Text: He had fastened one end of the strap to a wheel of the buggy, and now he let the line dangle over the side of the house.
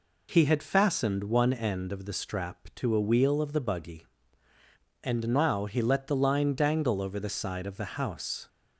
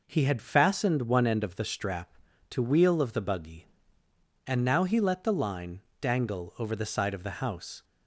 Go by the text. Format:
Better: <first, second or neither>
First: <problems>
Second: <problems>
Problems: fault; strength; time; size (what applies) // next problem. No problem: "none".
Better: first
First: none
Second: skips "a"; at 2.6 s // pauses between "line" and "dangle"; slight; at 5.7 s; 0.20 s long